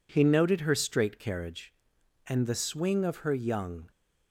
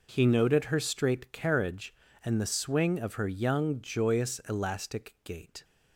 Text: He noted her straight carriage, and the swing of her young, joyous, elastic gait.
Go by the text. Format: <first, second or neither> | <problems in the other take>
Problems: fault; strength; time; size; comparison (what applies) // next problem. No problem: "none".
second | stops before "joyous elastic gait"; at 3.9 s